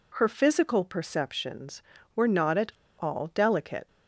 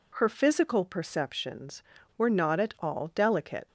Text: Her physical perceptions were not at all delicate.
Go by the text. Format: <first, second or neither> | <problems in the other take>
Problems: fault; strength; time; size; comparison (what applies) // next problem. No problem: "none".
second | pauses between "at" and "all"; slight; at 2.7 s; 0.27 s long